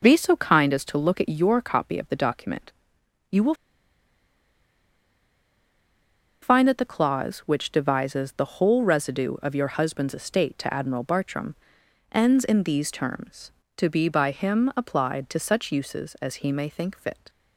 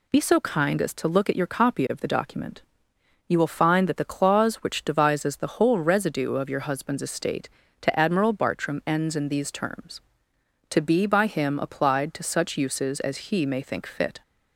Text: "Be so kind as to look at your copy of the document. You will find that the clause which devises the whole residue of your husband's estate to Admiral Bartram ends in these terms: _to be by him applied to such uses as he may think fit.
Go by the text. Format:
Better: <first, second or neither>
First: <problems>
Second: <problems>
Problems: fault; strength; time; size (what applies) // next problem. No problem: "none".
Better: second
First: pauses between "will" and "find"; strong; at 3.5 s; 2.8 s long // pauses between "Bartram" and "ends"; noticeable; at 11.5 s; 0.56 s long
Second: none